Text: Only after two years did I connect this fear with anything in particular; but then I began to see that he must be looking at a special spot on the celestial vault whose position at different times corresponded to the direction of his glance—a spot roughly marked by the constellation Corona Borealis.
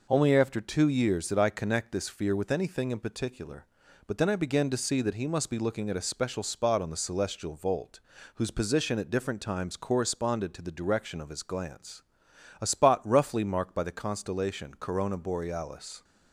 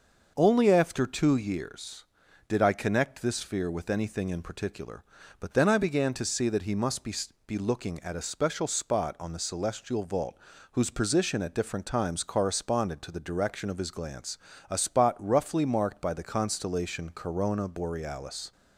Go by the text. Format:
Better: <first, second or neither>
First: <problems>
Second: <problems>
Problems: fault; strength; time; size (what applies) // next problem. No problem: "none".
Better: first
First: pauses between "vault" and "whose"; slight; at 7.9 s; 0.34 s long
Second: starts louder than the rest; noticeable; until 1.3 s; 6 dB // says "be" twice; at 7.4 s // pauses between "vault" and "whose"; slight; at 10.3 s; 0.36 s long